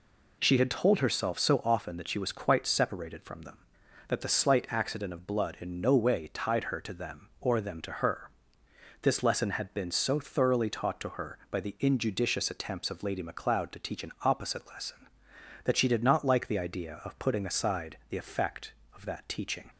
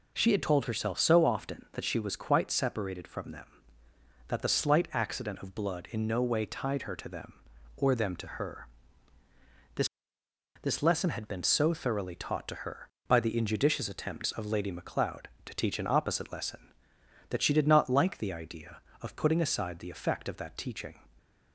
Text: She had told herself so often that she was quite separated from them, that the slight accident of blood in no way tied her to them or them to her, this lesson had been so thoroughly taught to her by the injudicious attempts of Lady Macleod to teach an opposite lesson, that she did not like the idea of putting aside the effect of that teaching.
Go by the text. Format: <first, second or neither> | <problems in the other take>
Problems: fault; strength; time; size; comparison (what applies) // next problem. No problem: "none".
first | says "this" twice; at 10.6 s